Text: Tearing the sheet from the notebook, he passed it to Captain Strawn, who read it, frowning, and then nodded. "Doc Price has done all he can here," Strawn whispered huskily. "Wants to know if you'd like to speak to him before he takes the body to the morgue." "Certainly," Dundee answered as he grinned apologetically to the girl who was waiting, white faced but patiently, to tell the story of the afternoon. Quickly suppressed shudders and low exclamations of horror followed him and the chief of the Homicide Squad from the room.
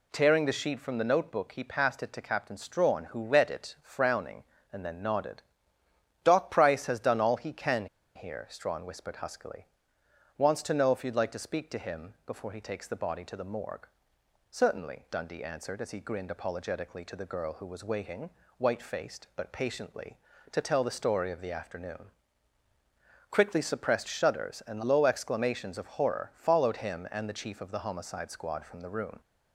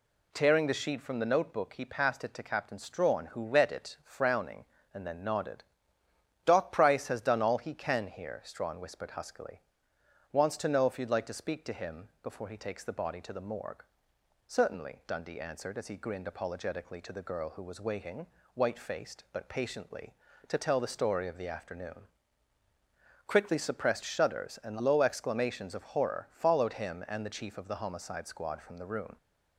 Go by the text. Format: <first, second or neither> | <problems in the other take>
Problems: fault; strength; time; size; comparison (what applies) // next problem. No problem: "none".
second | pauses between "can" and "here"; slight; at 7.8 s; 0.29 s long